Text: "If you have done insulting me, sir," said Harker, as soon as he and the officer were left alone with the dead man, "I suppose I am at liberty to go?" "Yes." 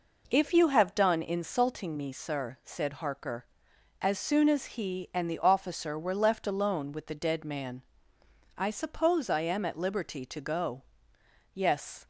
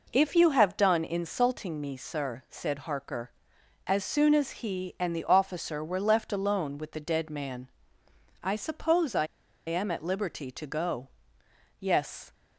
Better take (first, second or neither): first